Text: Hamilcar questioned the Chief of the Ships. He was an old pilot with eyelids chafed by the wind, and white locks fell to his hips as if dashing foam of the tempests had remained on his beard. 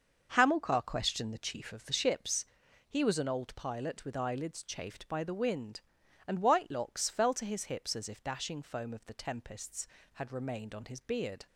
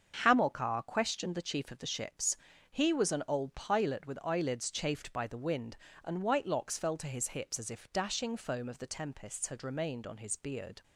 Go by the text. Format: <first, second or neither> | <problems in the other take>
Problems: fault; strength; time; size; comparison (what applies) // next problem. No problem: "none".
neither | starts louder than the rest; the same in both